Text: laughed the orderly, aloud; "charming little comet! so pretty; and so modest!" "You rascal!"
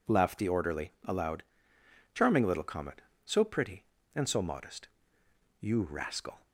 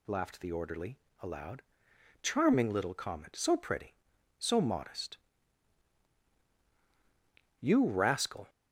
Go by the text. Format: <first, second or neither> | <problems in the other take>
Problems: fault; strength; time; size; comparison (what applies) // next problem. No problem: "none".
first | skips "and"; at 4.1 s